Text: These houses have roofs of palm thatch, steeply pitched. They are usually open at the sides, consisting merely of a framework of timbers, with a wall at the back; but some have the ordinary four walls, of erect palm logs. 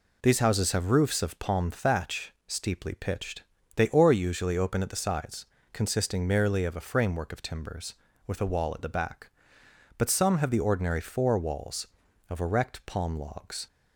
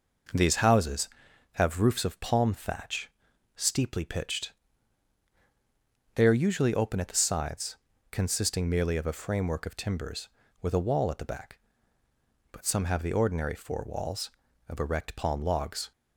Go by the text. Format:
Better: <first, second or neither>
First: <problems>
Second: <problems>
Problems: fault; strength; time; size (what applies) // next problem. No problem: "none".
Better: second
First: says "or" for "are"; at 3.8 s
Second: none